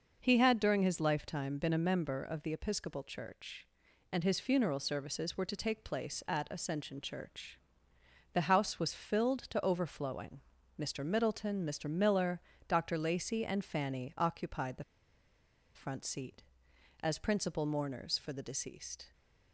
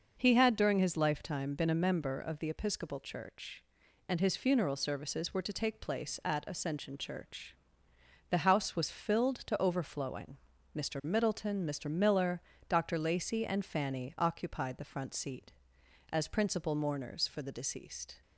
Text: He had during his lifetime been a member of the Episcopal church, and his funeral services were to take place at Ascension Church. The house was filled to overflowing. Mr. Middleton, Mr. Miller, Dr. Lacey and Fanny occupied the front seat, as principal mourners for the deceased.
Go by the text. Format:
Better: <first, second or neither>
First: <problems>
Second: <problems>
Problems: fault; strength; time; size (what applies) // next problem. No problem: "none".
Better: second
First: pauses between "the" and "front"; noticeable; at 14.8 s; 0.92 s long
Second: none